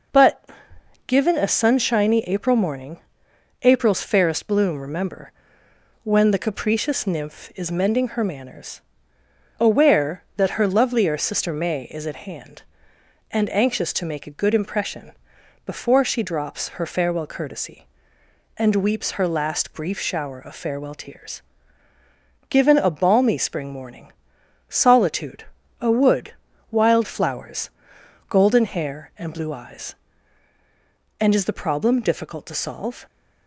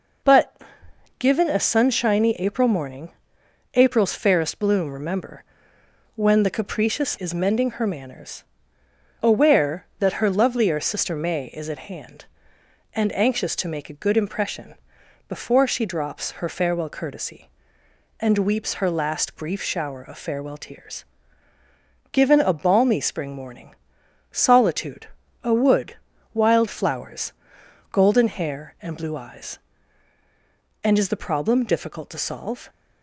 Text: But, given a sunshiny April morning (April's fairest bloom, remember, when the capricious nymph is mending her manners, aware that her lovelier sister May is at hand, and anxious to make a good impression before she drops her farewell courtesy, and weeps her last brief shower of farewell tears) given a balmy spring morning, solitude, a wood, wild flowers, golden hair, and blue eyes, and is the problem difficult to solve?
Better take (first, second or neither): first